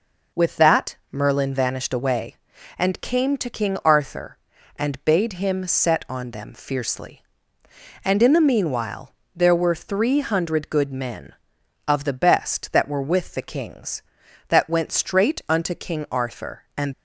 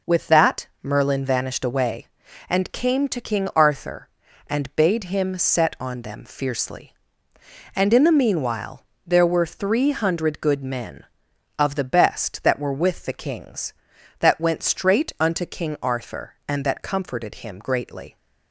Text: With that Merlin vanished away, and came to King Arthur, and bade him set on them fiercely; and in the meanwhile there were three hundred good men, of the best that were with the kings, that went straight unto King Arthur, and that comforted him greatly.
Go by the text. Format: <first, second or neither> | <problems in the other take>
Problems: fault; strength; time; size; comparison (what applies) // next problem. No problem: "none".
second | pauses between "meanwhile" and "there"; slight; at 9.1 s; 0.22 s long; slight in the second // stops before "that comforted him greatly"; at 16.9 s